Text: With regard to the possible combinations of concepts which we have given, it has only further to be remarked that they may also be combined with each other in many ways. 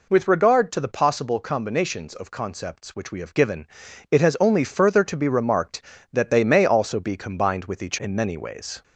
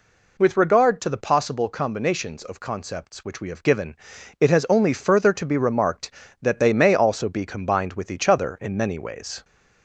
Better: second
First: skips "other"; at 7.9 s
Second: none

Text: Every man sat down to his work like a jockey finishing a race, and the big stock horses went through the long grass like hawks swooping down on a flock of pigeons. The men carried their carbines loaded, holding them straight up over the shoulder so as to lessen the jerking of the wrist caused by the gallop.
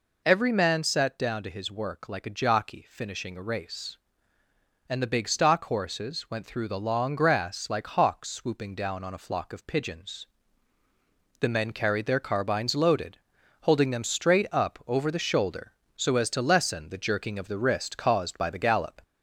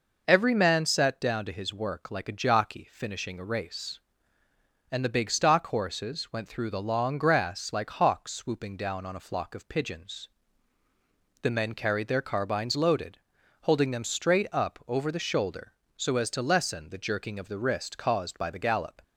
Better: second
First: gets louder; slight; throughout; 2 dB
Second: none

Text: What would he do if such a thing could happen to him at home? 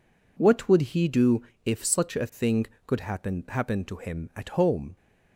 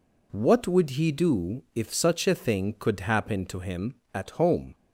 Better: second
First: pauses between "do" and "if"; slight; at 1.4 s; 0.24 s long // says "happen" twice; at 3.4 s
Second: none

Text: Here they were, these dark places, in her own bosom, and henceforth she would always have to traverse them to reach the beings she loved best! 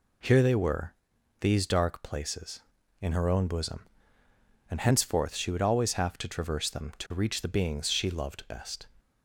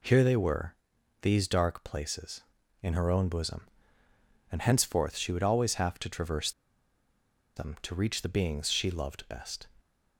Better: first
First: none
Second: pauses between "traverse" and "them"; at 6.5 s; 1.0 s long

